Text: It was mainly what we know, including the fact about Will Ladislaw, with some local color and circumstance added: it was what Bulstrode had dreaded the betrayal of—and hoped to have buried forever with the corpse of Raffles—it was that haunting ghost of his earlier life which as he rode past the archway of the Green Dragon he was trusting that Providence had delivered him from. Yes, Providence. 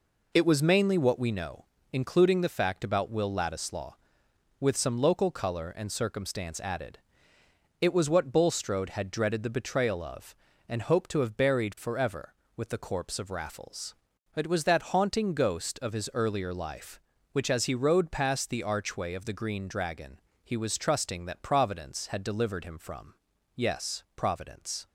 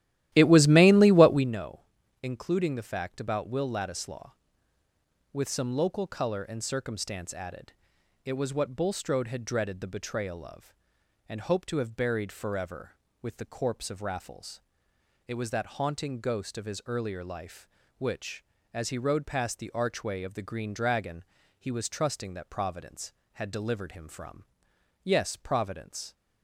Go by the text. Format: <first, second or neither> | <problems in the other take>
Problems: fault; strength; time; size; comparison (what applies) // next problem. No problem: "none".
first | starts louder than the rest; strong; until 1.6 s; 14 dB // pauses between "Dragon" and "he"; slight; at 21.2 s; 0.34 s long; slight in the first